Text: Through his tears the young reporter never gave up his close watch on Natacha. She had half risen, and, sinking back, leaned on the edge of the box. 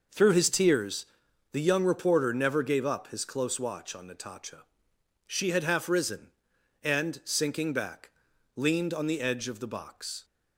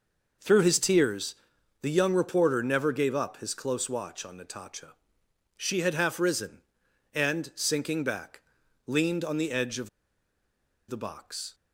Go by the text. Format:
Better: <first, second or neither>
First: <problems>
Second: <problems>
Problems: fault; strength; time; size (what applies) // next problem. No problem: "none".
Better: first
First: pauses between "tears" and "the"; noticeable; at 1.0 s; 0.46 s long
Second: pauses between "tears" and "the"; noticeable; at 1.3 s; 0.46 s long // pauses between "of" and "the"; at 9.8 s; 0.99 s long